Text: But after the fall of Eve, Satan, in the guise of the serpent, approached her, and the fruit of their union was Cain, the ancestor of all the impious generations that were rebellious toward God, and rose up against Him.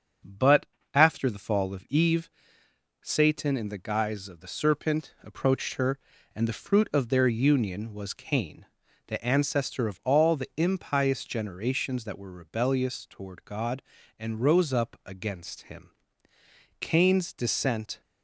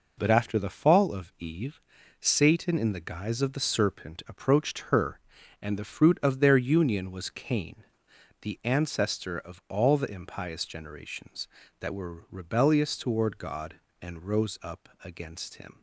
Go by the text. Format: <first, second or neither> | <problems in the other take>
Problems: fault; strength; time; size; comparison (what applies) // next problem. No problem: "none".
second | starts louder than the rest; until 1.5 s; 6.5 dB // pauses between "But" and "after"; slight; at 0.6 s; 0.26 s long // goes on to say "Cain's descent"; noticeable; from 16.8 s on; 1.2 s long